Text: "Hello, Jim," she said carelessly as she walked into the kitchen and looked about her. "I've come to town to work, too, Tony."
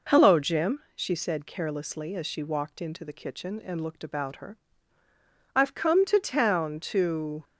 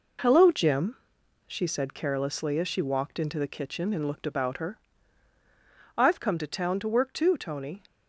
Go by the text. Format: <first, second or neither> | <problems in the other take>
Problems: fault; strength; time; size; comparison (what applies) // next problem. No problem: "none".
second | stops before "work too Tony"; at 7.4 s